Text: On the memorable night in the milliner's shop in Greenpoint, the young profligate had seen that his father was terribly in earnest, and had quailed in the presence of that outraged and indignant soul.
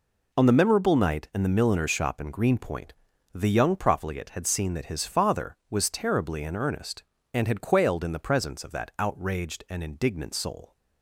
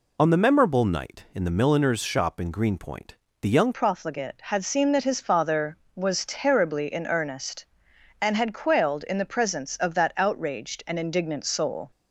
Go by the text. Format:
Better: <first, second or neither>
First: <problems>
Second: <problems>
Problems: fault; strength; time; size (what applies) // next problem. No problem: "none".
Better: first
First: none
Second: changes voice at "profligate"; from 3.7 s on; 8.2 s long